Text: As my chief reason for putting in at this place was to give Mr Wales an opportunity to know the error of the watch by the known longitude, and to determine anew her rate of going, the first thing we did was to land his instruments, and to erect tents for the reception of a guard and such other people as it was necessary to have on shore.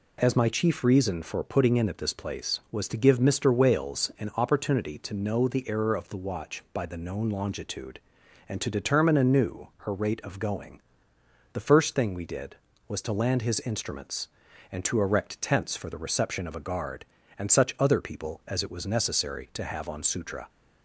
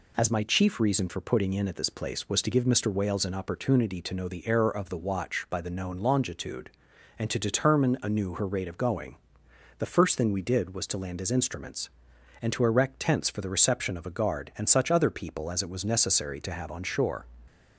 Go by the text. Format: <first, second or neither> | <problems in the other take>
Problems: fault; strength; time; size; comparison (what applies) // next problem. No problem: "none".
second | says "sutra" for "shore"; at 20.0 s